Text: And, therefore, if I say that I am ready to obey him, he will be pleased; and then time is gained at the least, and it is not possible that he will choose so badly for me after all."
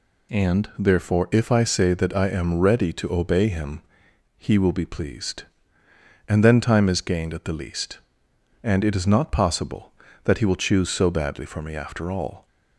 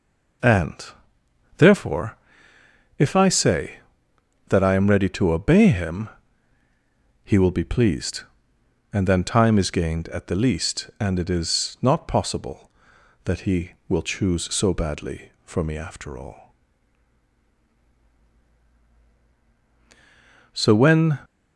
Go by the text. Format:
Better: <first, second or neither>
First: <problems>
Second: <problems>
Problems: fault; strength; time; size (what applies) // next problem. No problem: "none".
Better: first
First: none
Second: goes on to say "So when"; noticeable; from 20.5 s on; 0.66 s long